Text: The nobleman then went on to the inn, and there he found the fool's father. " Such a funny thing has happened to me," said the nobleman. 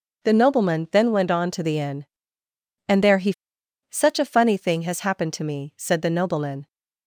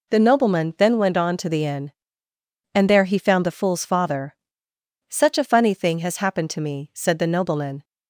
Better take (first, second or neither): second